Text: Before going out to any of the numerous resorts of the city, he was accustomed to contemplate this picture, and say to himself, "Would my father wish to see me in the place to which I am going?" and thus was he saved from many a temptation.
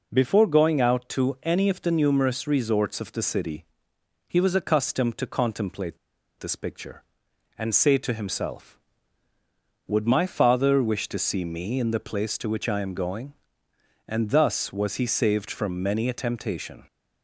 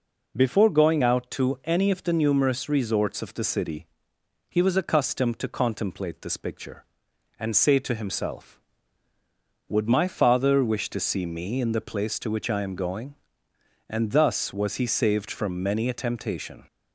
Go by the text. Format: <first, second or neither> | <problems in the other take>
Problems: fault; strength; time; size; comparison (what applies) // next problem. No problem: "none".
second | pauses between "contemplate" and "this"; at 5.9 s; 0.40 s long